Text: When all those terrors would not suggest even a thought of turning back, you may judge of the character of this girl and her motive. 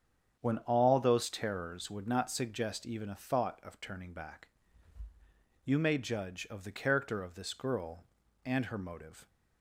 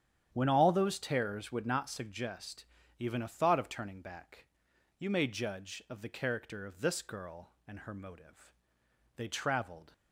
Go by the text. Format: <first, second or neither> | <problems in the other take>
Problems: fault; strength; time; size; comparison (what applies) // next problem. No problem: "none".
first | starts louder than the rest; strong; until 1.3 s; 9.5 dB; strong in the first // pauses between "suggest" and "even"; slight; at 2.6 s; 0.34 s long // goes on to say "They traveled"; noticeable; from 9.1 s on; 0.76 s long